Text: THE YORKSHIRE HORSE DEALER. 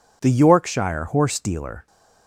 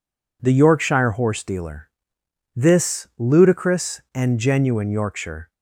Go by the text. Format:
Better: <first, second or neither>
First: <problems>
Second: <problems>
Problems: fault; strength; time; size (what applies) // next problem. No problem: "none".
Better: first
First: none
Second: goes on to say "THIS ludicrous and genuine Yorkshire"; strong; from 2.5 s on; 2.9 s long